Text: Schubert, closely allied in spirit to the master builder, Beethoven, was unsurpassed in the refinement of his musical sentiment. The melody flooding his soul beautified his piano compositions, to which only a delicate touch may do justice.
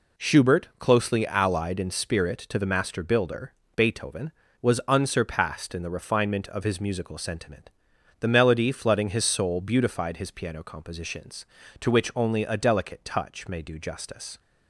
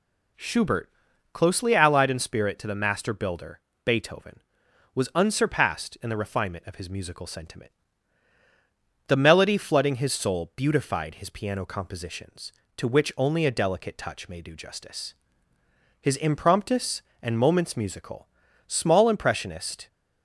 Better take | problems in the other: first | goes on to say "His Impromptus and Moments Musical small impressionist"; strong; from 16.0 s on; 3.8 s long

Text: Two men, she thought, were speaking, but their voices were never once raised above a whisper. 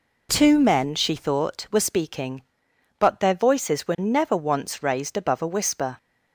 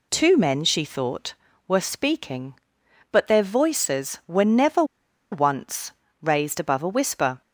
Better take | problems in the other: first | pauses between "never" and "once"; noticeable; at 4.8 s; 0.47 s long // pauses between "once" and "raised"; slight; at 5.9 s; 0.30 s long

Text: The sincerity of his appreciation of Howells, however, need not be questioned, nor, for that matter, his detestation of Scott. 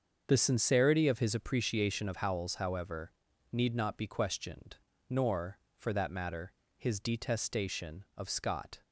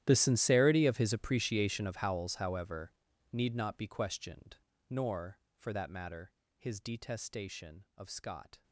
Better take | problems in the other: first | gets quieter; strong; throughout; 22 dB // starts louder than the rest; strong; until 1.0 s; 12 dB; also in the first

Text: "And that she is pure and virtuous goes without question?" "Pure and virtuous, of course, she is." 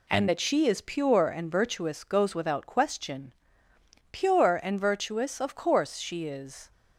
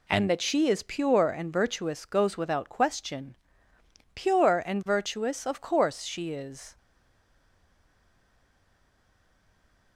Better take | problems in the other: first | stays silent after the last word; strong; from 6.7 s on; 3.2 s long

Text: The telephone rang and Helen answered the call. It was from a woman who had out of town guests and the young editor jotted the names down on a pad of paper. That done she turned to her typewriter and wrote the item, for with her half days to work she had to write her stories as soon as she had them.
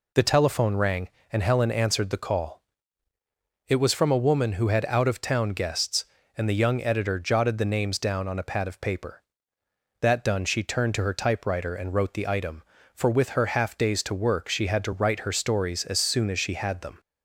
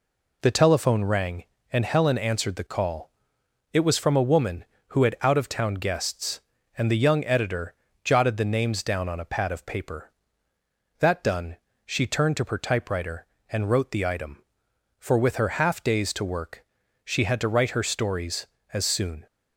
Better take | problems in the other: first | pauses between "editor" and "jotted"; slight; at 7.7 s; 0.30 s long // pauses between "done" and "she"; slight; at 11.5 s; 0.28 s long // pauses between "work" and "she"; at 16.6 s; 0.40 s long // stops before "as she had them"; at 19.2 s

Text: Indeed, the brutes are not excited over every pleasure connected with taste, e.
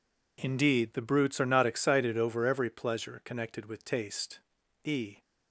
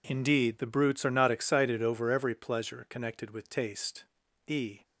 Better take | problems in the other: neither | none

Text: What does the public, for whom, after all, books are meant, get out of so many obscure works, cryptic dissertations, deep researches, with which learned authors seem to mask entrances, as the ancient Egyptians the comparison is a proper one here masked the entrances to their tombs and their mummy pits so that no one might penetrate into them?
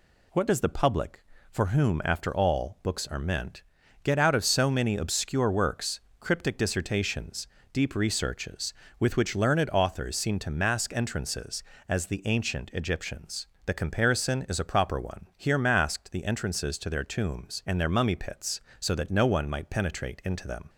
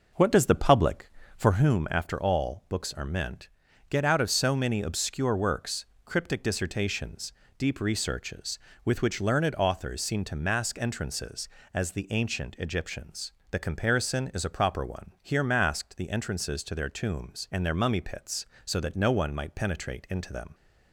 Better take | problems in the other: first | starts louder than the rest; noticeable; until 1.8 s; 5.5 dB // pauses between "Egyptians" and "the"; slight; at 13.3 s; 0.20 s long; slight in the first

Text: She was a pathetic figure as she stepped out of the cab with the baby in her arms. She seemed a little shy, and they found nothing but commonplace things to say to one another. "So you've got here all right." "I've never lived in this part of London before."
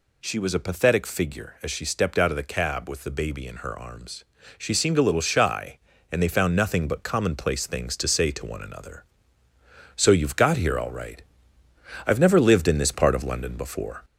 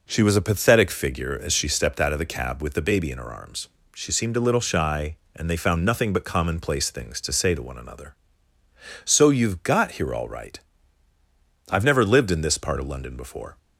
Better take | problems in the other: second | gets louder; slight; throughout; 2 dB

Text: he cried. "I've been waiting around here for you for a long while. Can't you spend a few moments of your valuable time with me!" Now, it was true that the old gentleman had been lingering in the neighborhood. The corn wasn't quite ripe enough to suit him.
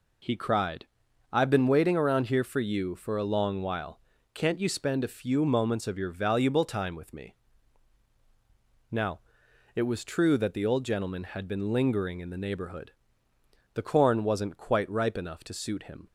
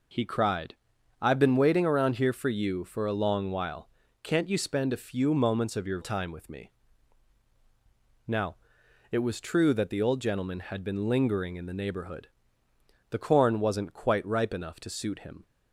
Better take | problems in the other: first | skips "valuable"; at 6.0 s

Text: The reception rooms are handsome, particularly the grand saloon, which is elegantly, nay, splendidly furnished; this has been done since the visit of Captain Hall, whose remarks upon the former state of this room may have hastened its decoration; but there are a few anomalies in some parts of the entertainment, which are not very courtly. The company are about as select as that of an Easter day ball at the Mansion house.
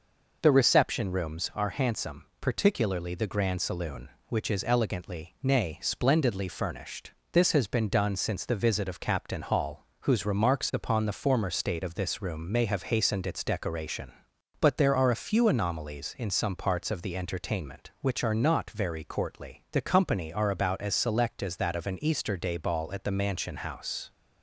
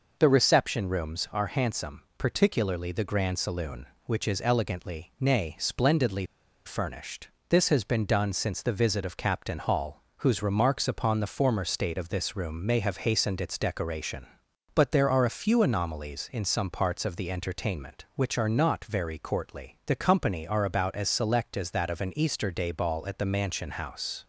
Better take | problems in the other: first | pauses between "splendidly" and "furnished"; at 6.2 s; 0.42 s long

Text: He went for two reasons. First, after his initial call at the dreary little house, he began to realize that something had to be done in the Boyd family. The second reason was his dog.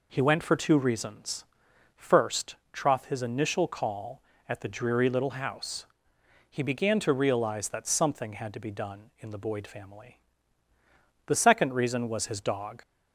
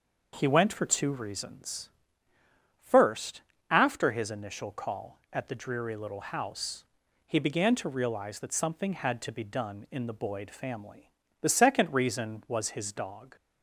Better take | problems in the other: second | says "troth" for "after"; at 2.7 s

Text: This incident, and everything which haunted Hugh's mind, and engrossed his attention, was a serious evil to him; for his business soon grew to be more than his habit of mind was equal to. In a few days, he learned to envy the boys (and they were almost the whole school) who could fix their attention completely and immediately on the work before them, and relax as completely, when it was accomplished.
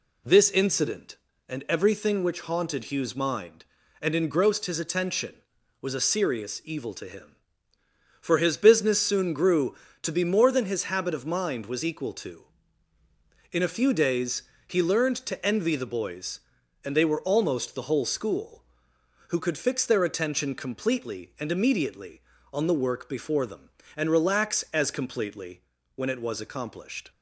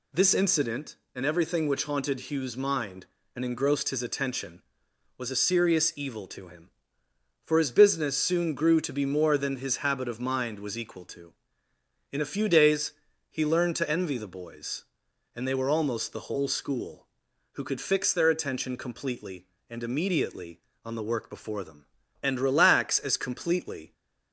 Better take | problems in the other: first | stops before "when it was accomplished"; at 23.9 s

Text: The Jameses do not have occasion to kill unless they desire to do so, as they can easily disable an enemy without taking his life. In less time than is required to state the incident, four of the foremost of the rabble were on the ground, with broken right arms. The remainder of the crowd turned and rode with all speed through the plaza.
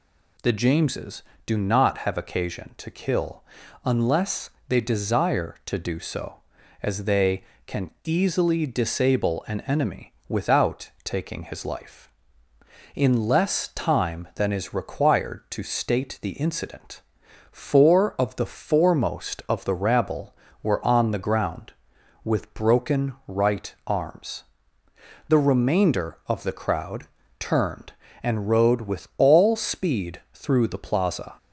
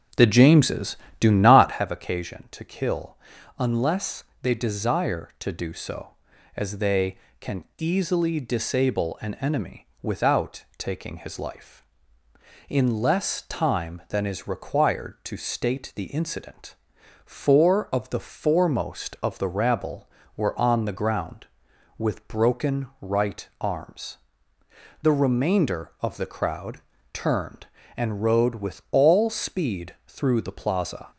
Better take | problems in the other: first | starts louder than the rest; until 1.9 s; 7 dB // pauses between "kill" and "unless"; at 3.1 s; 0.42 s long; also in the first // pauses between "unless" and "they"; slight; at 4.2 s; 0.18 s long; slight in the first // pauses between "enemy" and "without"; slight; at 9.8 s; 0.16 s long; slight in the first // pauses between "broken" and "right"; slight; at 22.8 s; 0.16 s long; slight in the first // pauses between "crowd" and "turned"; slight; at 26.7 s; 0.34 s long; slight in the first

